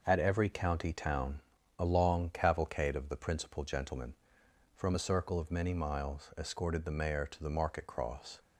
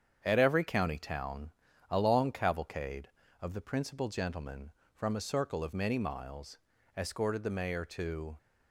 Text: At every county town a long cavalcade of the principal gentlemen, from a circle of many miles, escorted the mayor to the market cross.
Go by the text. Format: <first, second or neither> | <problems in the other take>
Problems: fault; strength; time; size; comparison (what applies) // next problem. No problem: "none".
first | starts louder than the rest; strong; until 1.2 s; 8 dB // pauses between "town" and "a"; at 1.5 s; 0.40 s long; also in the first // stops before "the market cross"; at 8.3 s